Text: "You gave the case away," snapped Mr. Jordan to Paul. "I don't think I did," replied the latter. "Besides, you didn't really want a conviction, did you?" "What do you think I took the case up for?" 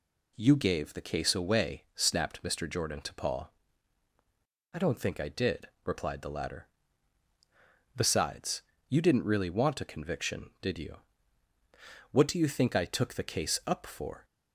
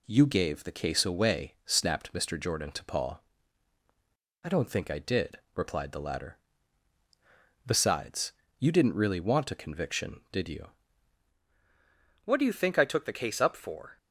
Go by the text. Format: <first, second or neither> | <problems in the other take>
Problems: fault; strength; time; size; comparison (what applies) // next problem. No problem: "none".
first | changes voice at "What"; from 12.2 s on; 1.7 s long